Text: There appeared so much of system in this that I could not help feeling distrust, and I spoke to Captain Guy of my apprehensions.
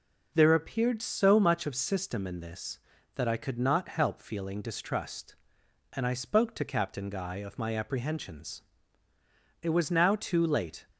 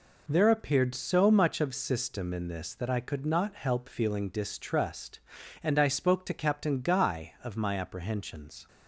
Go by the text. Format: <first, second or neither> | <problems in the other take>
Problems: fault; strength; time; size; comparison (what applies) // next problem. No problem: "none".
second | goes on to say "It was now too late"; noticeable; from 9.6 s on; 1.2 s long